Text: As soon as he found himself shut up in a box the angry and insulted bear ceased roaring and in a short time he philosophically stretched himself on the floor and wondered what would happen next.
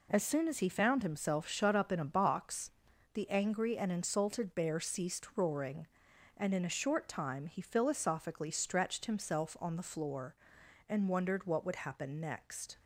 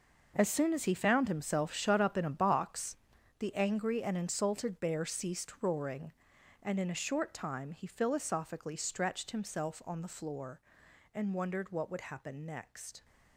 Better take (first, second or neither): first